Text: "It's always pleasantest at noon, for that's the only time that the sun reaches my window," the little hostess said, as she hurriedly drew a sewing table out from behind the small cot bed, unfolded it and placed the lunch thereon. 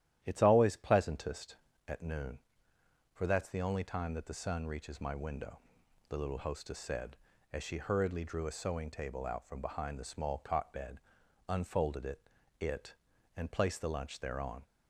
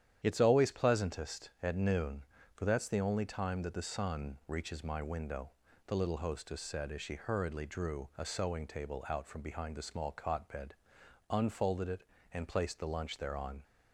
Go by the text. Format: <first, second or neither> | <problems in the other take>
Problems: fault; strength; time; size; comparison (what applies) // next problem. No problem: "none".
second | starts louder than the rest; strong; until 1.2 s; 12 dB; strong in the second // says "it" twice; at 12.5 s